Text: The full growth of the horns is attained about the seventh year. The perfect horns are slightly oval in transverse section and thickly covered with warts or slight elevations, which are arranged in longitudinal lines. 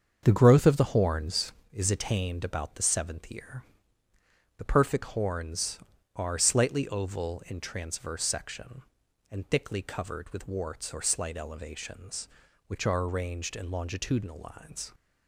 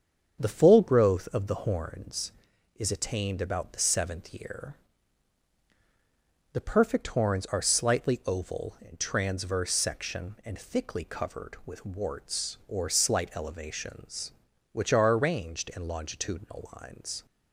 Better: second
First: starts louder than the rest; until 1.2 s; 7 dB // skips "full"; at 0.4 s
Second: starts louder than the rest; strong; until 1.4 s; 7.5 dB

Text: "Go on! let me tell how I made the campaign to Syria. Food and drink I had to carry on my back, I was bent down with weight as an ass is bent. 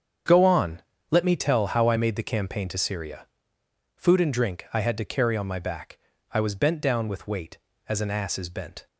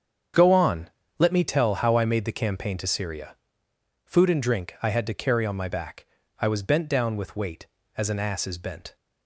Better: neither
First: starts louder than the rest; strong; until 1.5 s; 7.5 dB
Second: starts louder than the rest; strong; until 1.6 s; 7.5 dB

